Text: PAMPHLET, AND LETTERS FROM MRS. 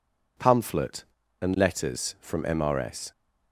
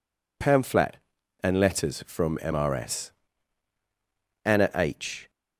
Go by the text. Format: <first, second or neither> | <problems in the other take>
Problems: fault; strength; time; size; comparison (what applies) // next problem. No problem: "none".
first | goes on to say "ANNA H"; noticeable; from 4.4 s on; 0.86 s long